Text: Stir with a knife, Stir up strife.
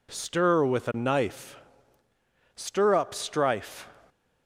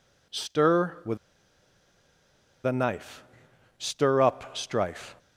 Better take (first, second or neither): first